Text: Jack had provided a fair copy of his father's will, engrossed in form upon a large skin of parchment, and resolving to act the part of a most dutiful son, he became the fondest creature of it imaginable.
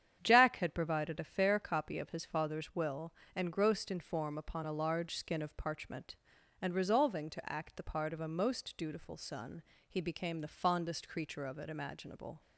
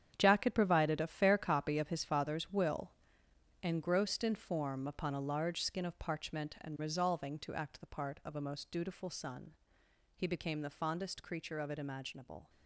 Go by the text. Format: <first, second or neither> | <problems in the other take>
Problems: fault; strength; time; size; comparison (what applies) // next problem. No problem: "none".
first | gets quieter; strong; throughout; 11.5 dB // starts louder than the rest; strong; until 1.1 s; 8.5 dB; strong in the first